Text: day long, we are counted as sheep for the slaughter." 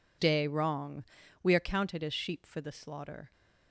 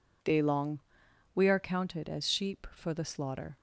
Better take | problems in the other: second | says "wrong" for "long"; at 0.4 s

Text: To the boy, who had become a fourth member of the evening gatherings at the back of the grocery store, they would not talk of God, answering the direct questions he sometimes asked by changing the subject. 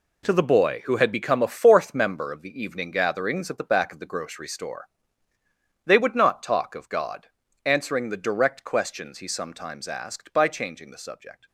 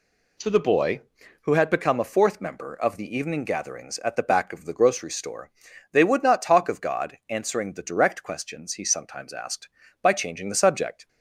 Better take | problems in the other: second | gets quieter; strong; throughout; 10.5 dB

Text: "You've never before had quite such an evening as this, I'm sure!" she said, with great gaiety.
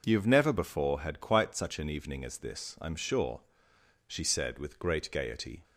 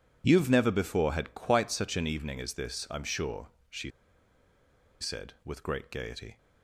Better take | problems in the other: first | pauses between "she" and "said"; at 3.9 s; 1.1 s long

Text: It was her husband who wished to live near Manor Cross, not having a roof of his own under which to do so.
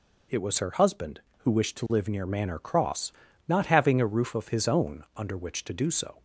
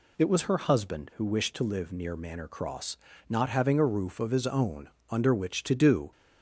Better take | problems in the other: first | pauses between "own" and "under"; slight; at 4.8 s; 0.20 s long // stops before "so"; at 6.1 s

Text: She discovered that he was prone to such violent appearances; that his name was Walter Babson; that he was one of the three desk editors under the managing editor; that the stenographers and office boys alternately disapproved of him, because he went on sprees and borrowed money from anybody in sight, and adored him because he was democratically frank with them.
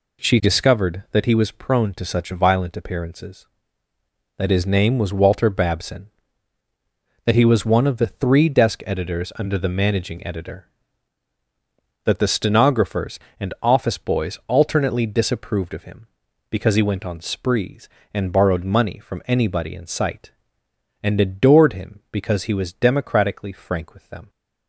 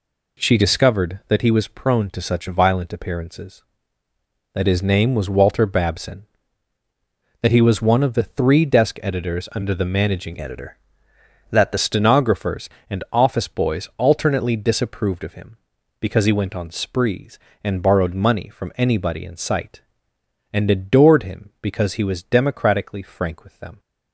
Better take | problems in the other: first | changes voice from "editor" to "the"; from 10.4 to 11.7 s; 1.3 s long

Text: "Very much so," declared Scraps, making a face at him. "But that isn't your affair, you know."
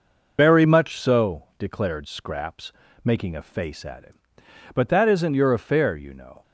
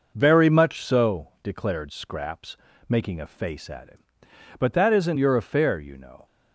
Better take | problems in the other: second | loses the start of "Very"; at 0.3 s; 75 ms

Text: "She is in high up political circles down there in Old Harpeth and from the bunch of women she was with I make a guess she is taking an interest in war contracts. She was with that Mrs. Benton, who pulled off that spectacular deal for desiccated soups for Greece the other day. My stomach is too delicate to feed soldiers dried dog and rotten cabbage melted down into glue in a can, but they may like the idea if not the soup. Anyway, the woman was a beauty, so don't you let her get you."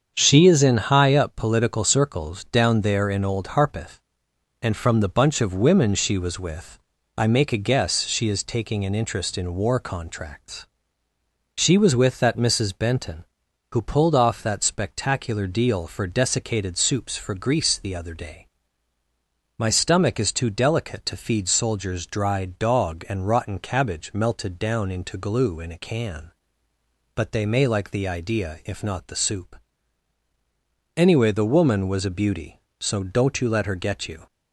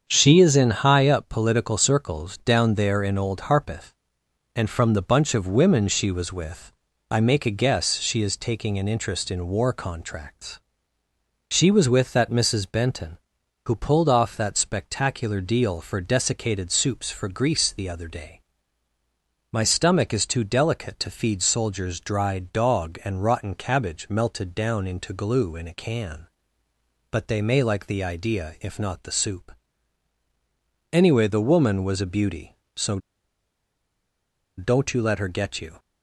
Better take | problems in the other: first | starts louder than the rest; strong; until 1.0 s; 7 dB; strong in the first // pauses between "with" and "I"; at 6.7 s; 0.38 s long; also in the first // pauses between "so" and "don't"; strong; at 32.9 s; 1.5 s long

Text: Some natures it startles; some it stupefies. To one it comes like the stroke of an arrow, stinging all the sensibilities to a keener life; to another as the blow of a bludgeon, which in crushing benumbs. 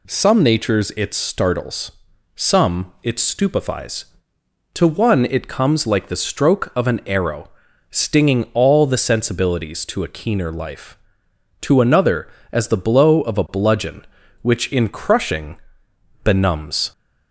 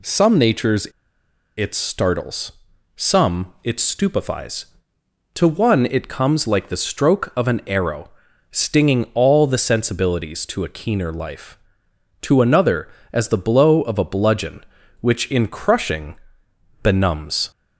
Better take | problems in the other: first | pauses between "natures" and "it"; noticeable; at 0.8 s; 0.69 s long // pauses between "crushing" and "benumbs"; noticeable; at 16.1 s; 0.66 s long; noticeable in the first

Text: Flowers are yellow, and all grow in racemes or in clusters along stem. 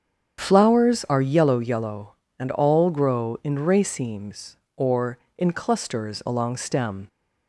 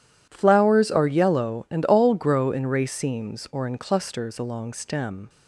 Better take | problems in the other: second | starts louder than the rest; strong; until 1.4 s; 8 dB // says "yellow" twice; at 1.5 s

